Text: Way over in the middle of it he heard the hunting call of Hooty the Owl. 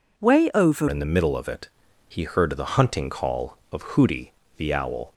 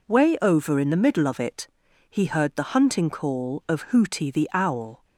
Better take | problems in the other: second | changes voice at "in"; from 0.8 s on; 4.3 s long // pauses between "it" and "he"; slight; at 1.6 s; 0.36 s long; also in the second // pauses between "Hooty" and "the"; slight; at 4.3 s; 0.24 s long

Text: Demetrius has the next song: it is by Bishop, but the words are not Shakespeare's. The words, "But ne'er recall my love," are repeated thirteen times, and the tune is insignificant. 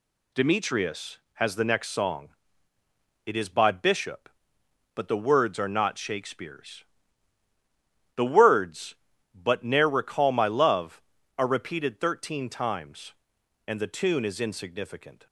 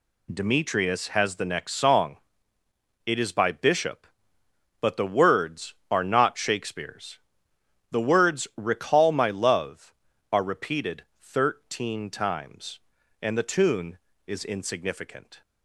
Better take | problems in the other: first | skips "But ne'er"; at 8.5 s // pauses between "repeated" and "thirteen"; slight; at 11.0 s; 0.16 s long

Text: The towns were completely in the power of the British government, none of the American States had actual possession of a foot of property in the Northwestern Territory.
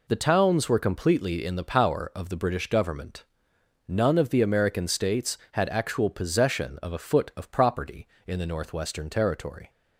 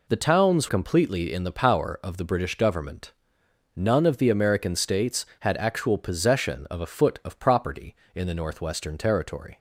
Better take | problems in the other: first | skips "were"; at 0.6 s

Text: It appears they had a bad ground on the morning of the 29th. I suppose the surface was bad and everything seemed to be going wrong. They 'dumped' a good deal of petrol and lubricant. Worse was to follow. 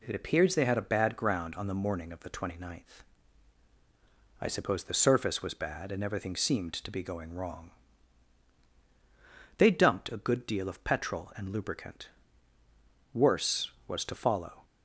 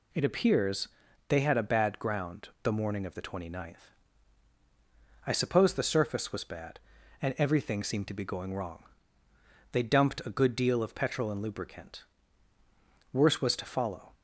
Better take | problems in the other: first | pauses between "appears" and "they"; at 0.8 s; 0.40 s long // skips "on"; at 2.5 s

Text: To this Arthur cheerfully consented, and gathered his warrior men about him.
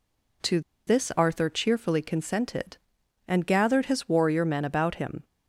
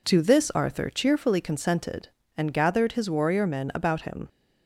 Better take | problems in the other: second | pauses between "To" and "this"; slight; at 0.5 s; 0.27 s long

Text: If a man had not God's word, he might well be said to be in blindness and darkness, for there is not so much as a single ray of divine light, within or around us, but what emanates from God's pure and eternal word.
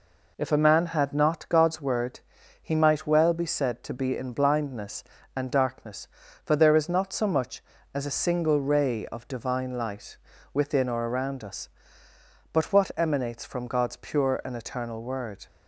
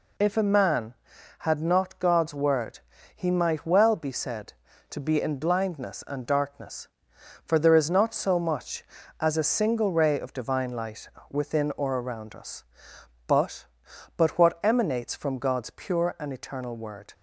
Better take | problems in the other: first | says "but" twice; at 14.1 s

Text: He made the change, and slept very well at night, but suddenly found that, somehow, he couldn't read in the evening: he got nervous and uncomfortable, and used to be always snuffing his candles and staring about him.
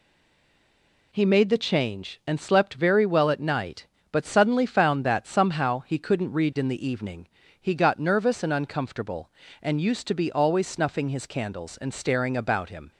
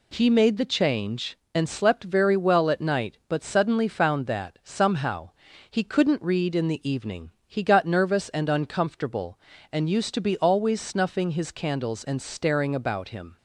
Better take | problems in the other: second | stays silent before the first word; until 1.1 s; 1.1 s long

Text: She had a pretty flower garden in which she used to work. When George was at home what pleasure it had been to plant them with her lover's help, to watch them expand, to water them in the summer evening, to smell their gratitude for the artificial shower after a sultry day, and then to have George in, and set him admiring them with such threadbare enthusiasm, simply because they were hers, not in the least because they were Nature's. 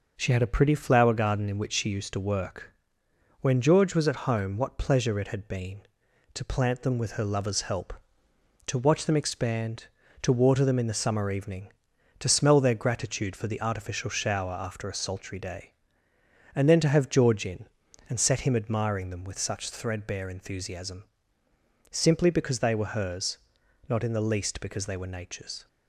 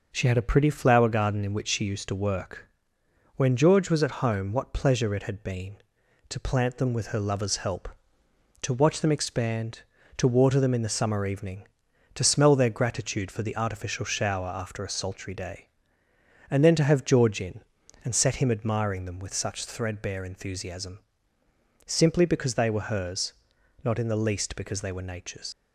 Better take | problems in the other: first | leaves "Nature's" unfinished; at 25.5 s; 100 ms

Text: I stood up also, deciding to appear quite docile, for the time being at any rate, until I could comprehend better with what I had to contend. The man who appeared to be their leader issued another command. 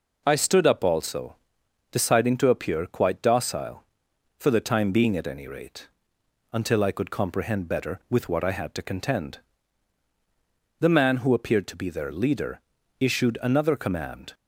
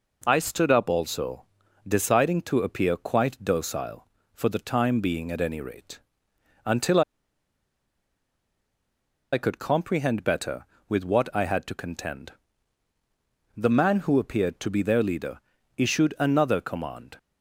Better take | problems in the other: first | pauses between "until" and "I"; strong; at 7.0 s; 2.3 s long // pauses between "leader" and "issued"; at 15.3 s; 0.38 s long; also in the first

